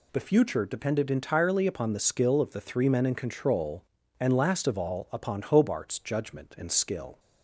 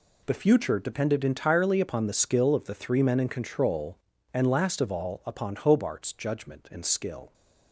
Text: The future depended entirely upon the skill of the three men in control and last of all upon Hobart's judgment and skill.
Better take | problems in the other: first | gets quieter; strong; throughout; 11.5 dB

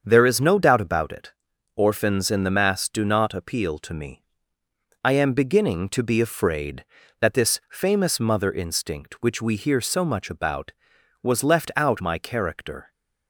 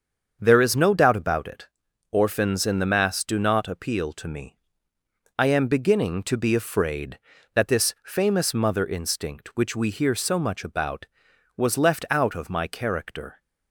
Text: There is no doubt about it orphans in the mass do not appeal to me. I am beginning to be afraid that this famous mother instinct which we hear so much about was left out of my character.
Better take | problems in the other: second | starts louder than the rest; until 1.0 s; 7 dB; also in the second // pauses between "it" and "orphans"; at 1.3 s; 0.44 s long; also in the second // skips "of"; at 11.9 s

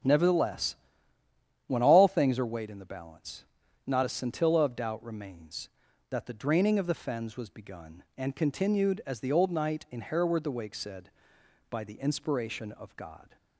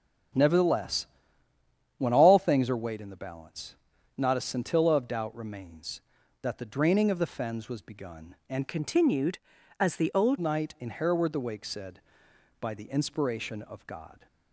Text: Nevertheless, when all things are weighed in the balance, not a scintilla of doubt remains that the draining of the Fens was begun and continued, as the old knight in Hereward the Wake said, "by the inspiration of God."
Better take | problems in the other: first | starts louder than the rest; until 2.2 s; 7 dB; strong in the first // changes voice from "continued" to "old"; from 8.6 to 10.3 s; 1.7 s long

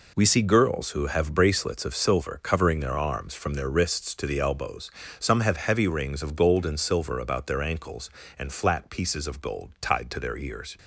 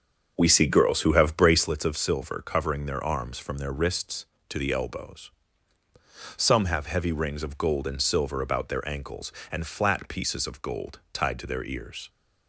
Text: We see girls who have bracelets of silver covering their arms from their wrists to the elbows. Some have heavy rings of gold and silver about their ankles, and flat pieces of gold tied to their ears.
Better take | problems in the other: first | starts louder than the rest; until 1.7 s; 6 dB

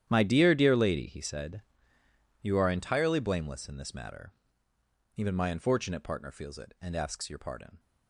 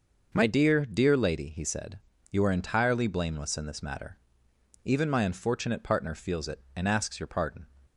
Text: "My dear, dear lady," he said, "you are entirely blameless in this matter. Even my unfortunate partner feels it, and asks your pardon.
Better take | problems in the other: second | gets quieter; strong; throughout; 15.5 dB

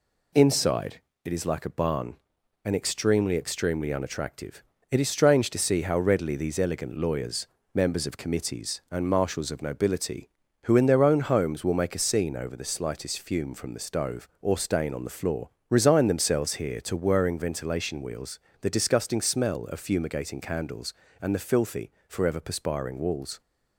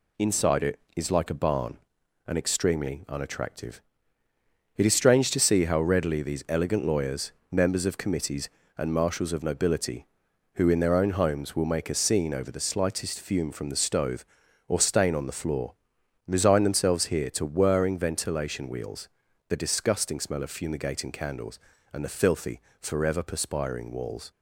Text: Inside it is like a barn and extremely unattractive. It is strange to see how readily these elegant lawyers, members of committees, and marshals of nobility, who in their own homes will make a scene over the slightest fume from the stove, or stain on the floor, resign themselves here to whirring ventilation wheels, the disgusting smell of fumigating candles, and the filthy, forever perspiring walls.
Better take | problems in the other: second | pauses between "Inside" and "it"; slight; at 1.0 s; 0.24 s long // says "extremely" twice; at 3.3 s

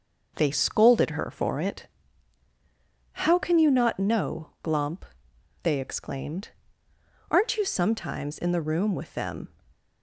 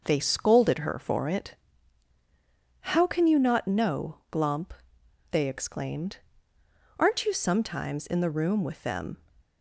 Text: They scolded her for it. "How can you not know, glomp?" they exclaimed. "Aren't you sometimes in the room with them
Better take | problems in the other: neither | none

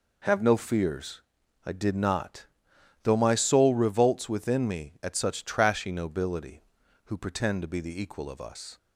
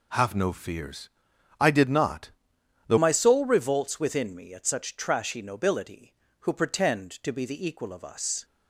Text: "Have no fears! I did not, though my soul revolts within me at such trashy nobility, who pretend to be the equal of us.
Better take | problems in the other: first | changes voice at "my"; from 2.9 s on; 5.5 s long

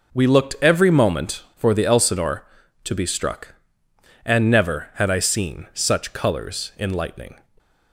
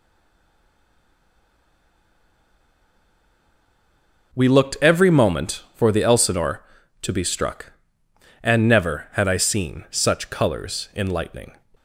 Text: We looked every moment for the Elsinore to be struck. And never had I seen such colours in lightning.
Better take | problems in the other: first | stays silent before the first word; strong; until 4.3 s; 4.3 s long

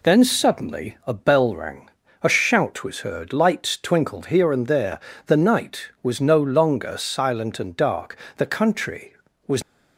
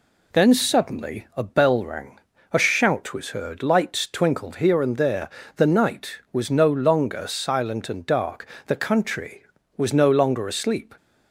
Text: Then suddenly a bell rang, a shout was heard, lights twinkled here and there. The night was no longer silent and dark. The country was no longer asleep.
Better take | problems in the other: second | stops before "no longer asleep"; at 9.6 s

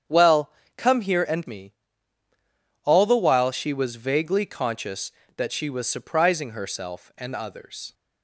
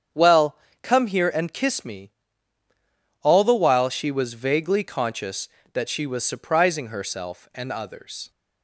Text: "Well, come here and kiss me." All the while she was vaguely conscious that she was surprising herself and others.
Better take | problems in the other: second | starts louder than the rest; strong; until 1.3 s; 8.5 dB; strong in the second // skips "kiss"; at 1.4 s

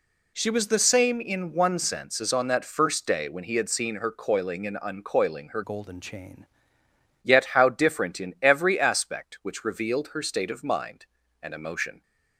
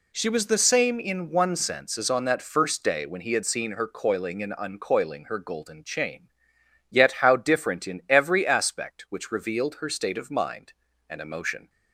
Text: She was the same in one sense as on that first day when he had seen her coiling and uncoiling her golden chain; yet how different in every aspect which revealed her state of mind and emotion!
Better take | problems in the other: second | changes voice from "golden" to "chain"; from 5.6 to 6.4 s; 0.8 s long

